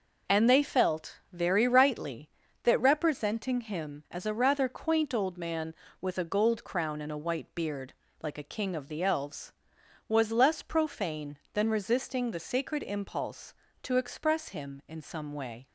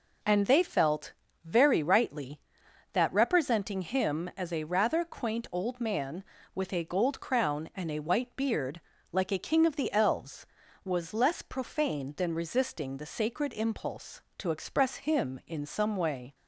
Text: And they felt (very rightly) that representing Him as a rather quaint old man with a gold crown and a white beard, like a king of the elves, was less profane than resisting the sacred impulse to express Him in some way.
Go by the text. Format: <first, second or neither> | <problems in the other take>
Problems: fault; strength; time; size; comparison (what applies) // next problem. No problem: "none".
neither | none